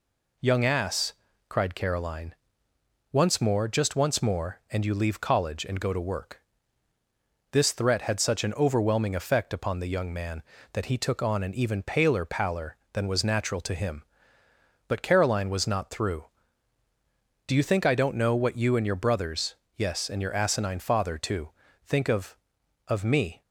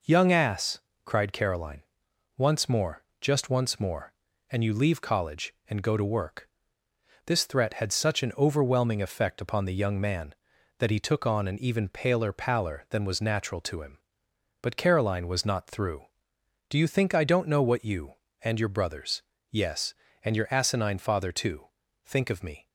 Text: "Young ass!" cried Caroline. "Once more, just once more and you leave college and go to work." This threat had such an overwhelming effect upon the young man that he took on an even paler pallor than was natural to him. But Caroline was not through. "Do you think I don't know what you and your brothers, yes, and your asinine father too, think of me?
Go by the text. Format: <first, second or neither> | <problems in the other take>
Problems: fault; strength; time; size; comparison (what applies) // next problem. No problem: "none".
second | says "of" twice; at 22.8 s